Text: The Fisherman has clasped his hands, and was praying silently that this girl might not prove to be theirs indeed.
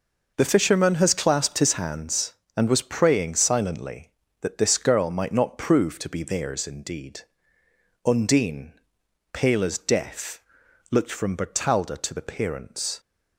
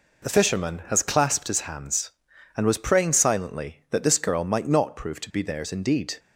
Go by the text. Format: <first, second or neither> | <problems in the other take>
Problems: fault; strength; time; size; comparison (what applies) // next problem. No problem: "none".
second | goes on to say "Undine pale as death looked from Bertalda to the parents"; strong; from 8.0 s on; 4.9 s long